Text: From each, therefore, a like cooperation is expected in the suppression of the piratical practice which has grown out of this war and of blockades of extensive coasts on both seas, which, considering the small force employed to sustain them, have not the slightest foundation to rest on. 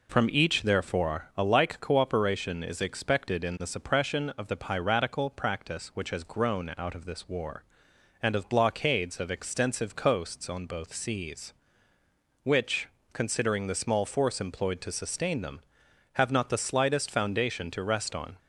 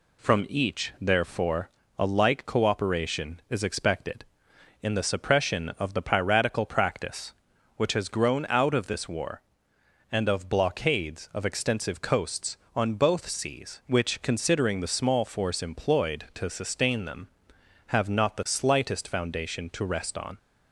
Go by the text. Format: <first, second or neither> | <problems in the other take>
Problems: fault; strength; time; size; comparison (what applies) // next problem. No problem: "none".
neither | none